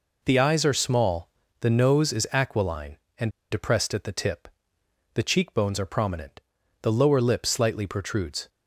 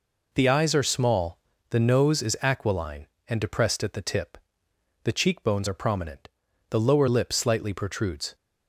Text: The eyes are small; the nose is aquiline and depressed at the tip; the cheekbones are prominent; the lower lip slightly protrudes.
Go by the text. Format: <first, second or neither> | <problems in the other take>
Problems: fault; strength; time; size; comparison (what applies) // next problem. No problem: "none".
second | pauses between "and" and "depressed"; slight; at 3.2 s; 0.23 s long